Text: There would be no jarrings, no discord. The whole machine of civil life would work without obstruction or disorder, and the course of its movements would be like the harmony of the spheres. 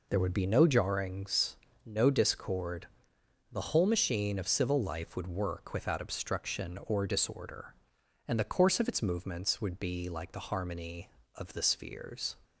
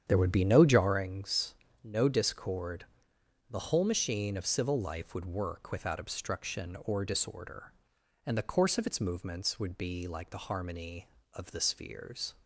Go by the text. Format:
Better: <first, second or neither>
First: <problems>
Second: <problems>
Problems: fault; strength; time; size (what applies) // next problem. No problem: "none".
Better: first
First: none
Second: starts louder than the rest; strong; until 1.1 s; 9 dB